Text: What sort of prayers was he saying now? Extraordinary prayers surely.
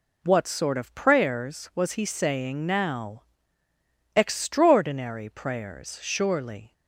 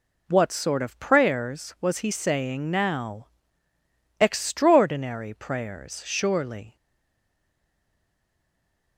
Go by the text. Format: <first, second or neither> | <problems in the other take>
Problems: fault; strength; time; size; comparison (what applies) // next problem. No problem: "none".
first | stays silent after the last word; from 6.7 s on; 2.2 s long